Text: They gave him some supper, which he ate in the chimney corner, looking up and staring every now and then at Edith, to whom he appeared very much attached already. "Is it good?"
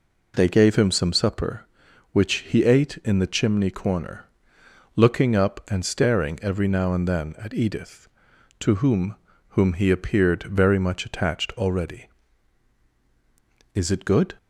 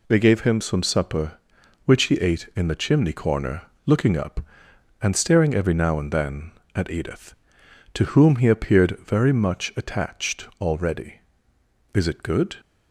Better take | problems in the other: second | says "whom" twice; at 9.4 s

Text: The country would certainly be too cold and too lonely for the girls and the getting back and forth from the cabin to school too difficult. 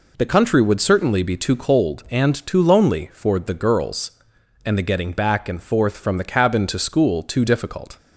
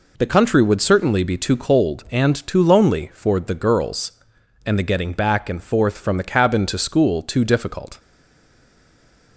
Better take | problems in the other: first | stays silent after the last word; noticeable; from 7.9 s on; 1.4 s long

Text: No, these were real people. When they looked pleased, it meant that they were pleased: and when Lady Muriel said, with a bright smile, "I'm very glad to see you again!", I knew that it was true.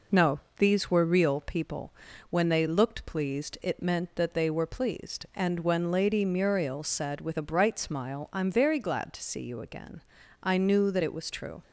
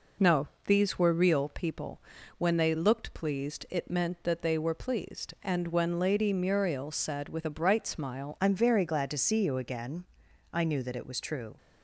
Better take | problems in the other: first | changes voice at "I'm"; from 8.3 s on; 3.2 s long

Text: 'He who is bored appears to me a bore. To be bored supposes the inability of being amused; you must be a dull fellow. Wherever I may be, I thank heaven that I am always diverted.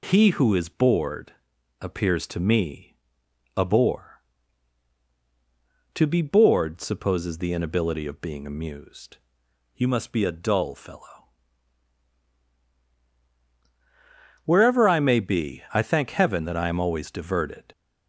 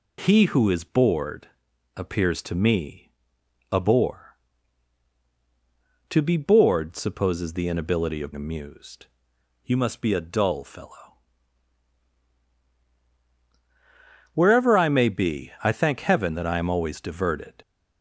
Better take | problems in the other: first | pauses between "bored" and "appears"; noticeable; at 1.4 s; 0.48 s long; noticeable in the first // pauses between "me" and "a"; noticeable; at 3.0 s; 0.62 s long; noticeable in the first // skips "being"; at 8.3 s

